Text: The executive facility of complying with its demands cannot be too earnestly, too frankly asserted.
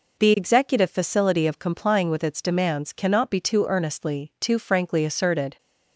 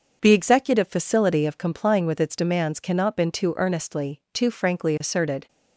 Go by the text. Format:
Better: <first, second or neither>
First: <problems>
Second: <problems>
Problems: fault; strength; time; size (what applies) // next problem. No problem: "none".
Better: first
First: none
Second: starts louder than the rest; until 1.2 s; 6 dB // says "been" for "be"; at 3.1 s